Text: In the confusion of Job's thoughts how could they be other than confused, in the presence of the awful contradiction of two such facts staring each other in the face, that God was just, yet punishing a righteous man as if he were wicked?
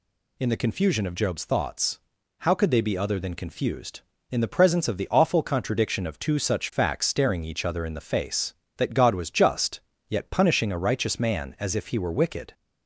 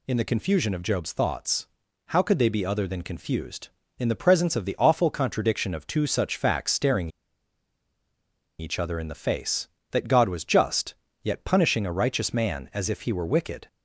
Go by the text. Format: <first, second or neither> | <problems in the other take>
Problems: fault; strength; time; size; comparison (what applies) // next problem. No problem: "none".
first | pauses between "thoughts" and "how"; at 1.6 s; 0.40 s long; also in the first // pauses between "staring" and "each"; strong; at 7.0 s; 1.5 s long